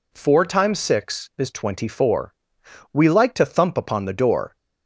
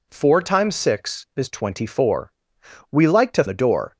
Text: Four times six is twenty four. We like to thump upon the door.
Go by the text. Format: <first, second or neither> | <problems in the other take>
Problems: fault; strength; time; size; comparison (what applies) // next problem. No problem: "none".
first | skips "thump upon"; at 3.4 s